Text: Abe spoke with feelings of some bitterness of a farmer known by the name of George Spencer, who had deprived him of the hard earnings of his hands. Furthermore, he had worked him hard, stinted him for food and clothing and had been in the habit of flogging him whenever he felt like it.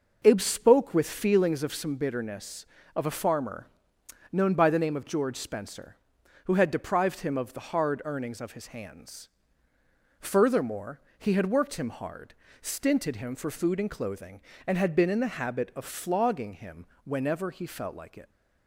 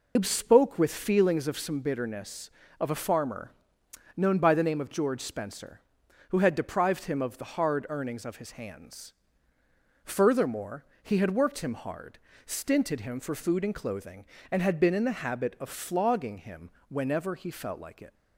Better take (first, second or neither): first